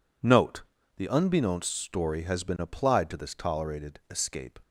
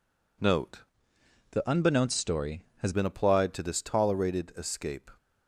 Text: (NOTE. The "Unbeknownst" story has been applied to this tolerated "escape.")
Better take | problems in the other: first | changes voice from "The" to "has"; from 1.5 to 2.9 s; 1.4 s long

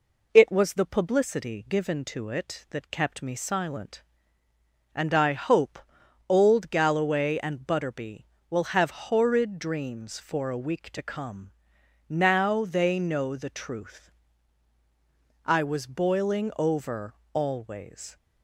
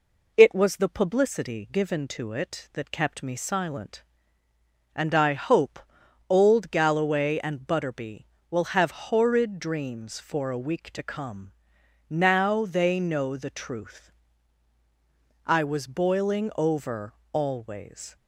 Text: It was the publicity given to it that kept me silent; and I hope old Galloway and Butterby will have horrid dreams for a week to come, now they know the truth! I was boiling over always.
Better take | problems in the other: neither | pauses between "hope" and "old"; noticeable; the same in both // pauses between "over" and "always"; slight; the same in both

